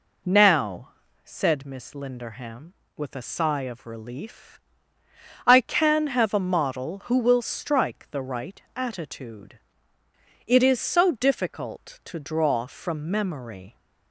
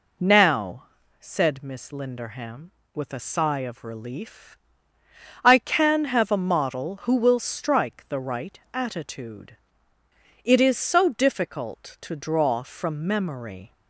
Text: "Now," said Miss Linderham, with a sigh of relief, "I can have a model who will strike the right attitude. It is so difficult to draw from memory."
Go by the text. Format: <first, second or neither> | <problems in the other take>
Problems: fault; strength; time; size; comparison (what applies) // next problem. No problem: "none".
neither | pauses between "right" and "attitude"; slight; the same in both